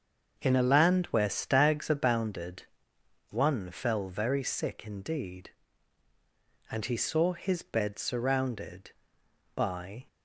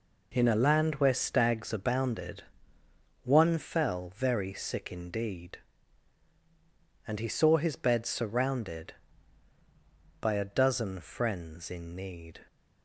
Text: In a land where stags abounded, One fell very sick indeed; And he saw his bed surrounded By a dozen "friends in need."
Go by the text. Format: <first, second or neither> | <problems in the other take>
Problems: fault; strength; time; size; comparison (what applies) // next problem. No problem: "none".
second | starts louder than the rest; until 1.3 s; 6.5 dB // stops before "a dozen friends in need"; at 10.0 s